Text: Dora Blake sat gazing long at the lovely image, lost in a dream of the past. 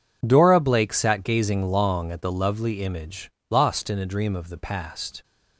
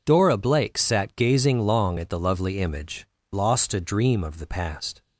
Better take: first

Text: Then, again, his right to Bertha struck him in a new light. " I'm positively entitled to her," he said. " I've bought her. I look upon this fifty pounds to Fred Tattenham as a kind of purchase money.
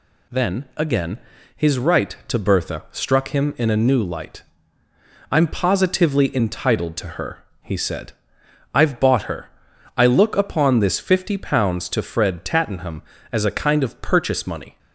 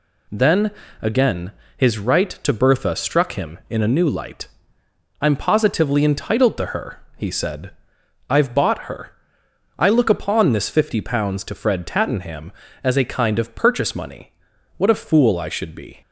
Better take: first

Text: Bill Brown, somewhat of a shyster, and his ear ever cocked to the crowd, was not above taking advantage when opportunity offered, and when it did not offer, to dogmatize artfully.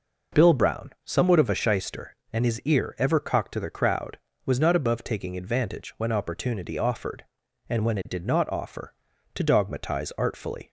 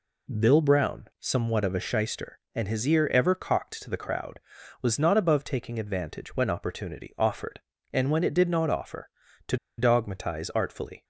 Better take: first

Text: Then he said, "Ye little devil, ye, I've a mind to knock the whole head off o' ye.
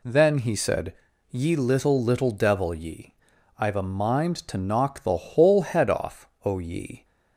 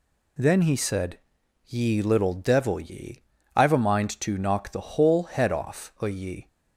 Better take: second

